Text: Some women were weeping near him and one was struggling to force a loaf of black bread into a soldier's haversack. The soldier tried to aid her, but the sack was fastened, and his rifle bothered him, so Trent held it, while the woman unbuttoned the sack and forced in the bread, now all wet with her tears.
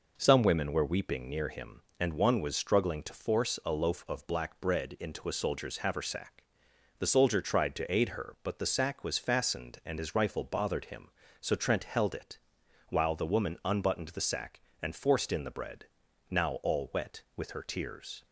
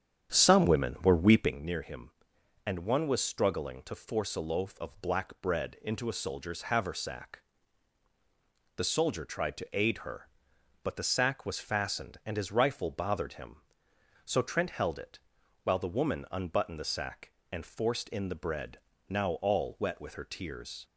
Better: first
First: none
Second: starts louder than the rest; strong; until 1.6 s; 9 dB

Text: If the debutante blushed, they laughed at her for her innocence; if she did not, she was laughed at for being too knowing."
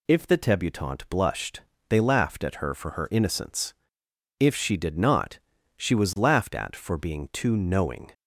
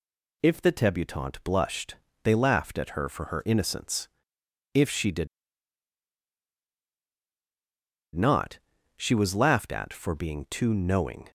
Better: first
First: none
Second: pauses between "did" and "not"; strong; at 5.2 s; 2.8 s long

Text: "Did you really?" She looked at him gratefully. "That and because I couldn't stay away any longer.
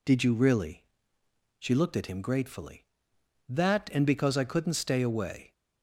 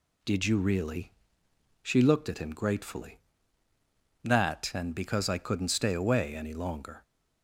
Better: second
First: stops before "any longer"; at 5.5 s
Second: none

